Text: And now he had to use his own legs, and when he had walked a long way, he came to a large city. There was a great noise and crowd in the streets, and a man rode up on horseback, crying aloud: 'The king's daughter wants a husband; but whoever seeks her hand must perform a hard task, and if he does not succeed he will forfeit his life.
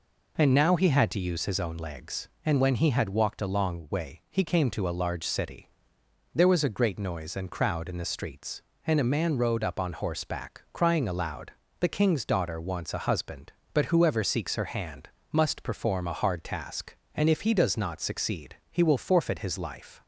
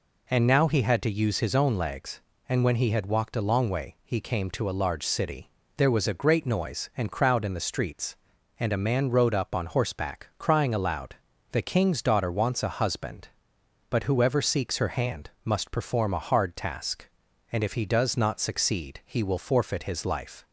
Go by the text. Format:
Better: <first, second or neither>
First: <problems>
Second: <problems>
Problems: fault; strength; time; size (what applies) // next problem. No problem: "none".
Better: neither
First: pauses between "hand" and "must"; slight; at 15.0 s; 0.24 s long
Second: pauses between "hand" and "must"; slight; at 15.2 s; 0.16 s long